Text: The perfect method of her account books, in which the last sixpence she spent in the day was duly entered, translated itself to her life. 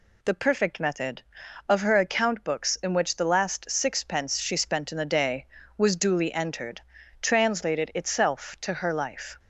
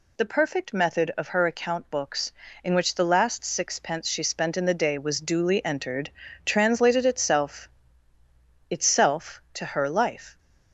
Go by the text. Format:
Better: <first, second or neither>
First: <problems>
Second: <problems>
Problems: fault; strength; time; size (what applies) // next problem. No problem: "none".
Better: first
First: none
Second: says "itself" twice; at 8.6 s